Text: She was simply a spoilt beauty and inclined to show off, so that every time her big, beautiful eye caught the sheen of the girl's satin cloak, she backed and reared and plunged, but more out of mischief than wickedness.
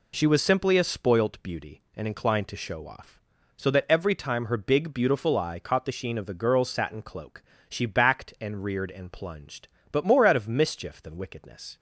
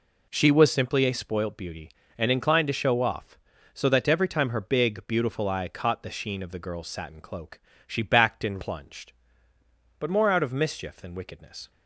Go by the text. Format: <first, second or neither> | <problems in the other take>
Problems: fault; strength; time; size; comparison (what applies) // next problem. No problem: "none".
first | skips "reared and"; at 8.6 s